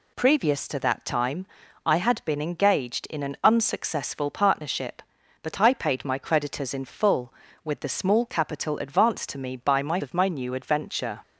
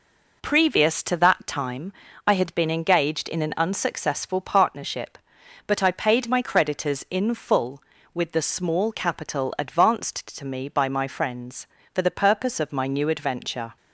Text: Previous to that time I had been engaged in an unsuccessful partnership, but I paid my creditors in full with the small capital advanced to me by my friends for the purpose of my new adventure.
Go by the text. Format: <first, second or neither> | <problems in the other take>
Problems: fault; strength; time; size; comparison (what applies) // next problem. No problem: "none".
second | pauses between "time" and "I"; at 1.4 s; 0.40 s long; slight in the second // skips "friends for the purpose"; at 10.0 s